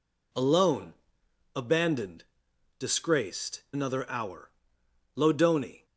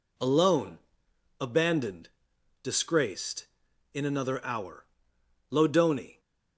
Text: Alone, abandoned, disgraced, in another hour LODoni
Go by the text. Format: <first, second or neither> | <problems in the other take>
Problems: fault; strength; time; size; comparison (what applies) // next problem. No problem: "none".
second | skips "in"; at 3.6 s // pauses between "hour" and "LODoni"; noticeable; at 4.5 s; 0.66 s long; noticeable in the second